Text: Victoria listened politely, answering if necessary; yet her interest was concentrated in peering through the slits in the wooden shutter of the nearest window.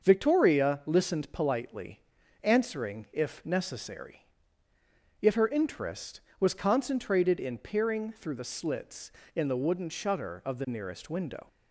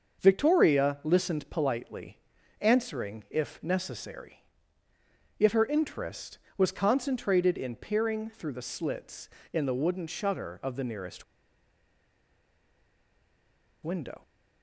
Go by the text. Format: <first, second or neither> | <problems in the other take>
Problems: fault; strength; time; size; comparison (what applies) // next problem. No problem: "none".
first | starts louder than the rest; until 1.2 s; 6.5 dB; also in the first // pauses between "nearest" and "window"; strong; at 11.2 s; 2.6 s long